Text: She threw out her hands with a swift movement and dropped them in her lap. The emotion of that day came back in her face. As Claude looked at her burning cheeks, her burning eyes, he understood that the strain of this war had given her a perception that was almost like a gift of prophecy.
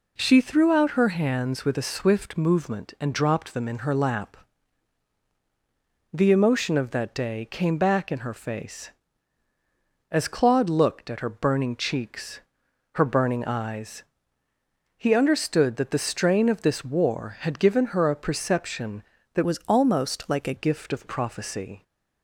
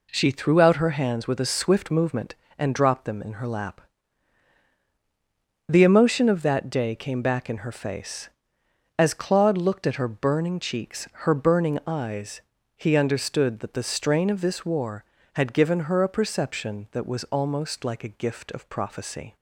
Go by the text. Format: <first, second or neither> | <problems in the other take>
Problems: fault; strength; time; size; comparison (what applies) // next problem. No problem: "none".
second | changes voice from "was" to "a"; from 19.4 to 20.5 s; 1.1 s long